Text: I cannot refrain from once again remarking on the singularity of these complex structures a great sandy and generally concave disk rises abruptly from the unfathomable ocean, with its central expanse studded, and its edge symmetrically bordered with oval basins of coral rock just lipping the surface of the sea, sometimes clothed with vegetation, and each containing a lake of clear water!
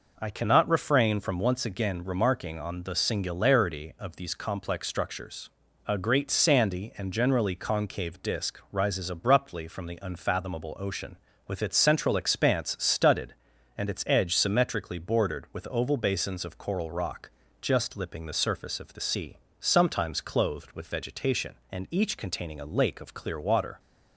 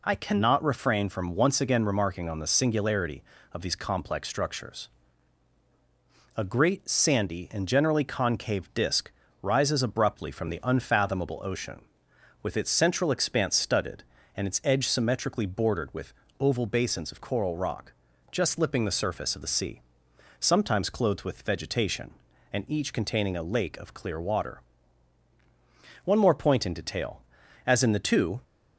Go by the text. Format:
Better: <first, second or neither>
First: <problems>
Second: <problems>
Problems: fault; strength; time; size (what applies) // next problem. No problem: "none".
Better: first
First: pauses between "structures" and "a"; slight; at 5.4 s; 0.36 s long // pauses between "rock" and "just"; slight; at 17.3 s; 0.30 s long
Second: pauses between "structures" and "a"; strong; at 4.8 s; 1.4 s long // pauses between "disk" and "rises"; slight; at 9.1 s; 0.28 s long // pauses between "with" and "oval"; slight; at 16.1 s; 0.28 s long // pauses between "rock" and "just"; at 17.9 s; 0.40 s long // goes on to say "One more point in detail as in the two"; strong; from 26.0 s on; 2.3 s long